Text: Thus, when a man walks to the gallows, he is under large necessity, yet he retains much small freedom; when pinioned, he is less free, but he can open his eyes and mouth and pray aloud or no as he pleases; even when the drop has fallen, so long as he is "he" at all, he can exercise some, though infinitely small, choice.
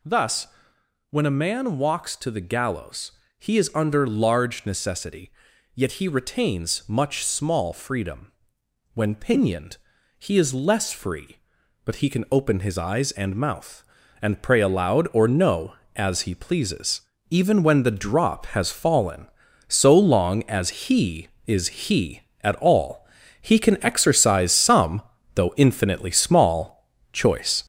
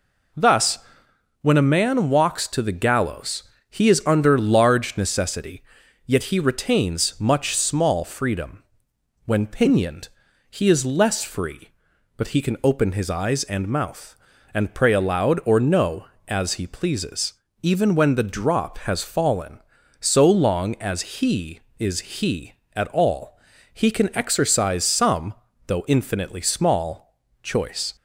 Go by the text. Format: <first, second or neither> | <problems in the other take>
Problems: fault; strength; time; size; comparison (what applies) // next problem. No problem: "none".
second | gets louder; noticeable; throughout; 5.5 dB // pauses between "is" and "he"; slight; at 21.6 s; 0.22 s long; slight in the second